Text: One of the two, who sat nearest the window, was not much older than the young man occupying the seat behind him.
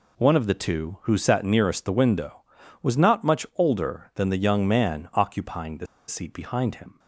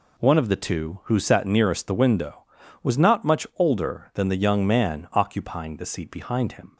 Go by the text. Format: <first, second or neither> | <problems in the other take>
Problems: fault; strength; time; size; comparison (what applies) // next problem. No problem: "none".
second | pauses between "the" and "seat"; slight; at 5.8 s; 0.22 s long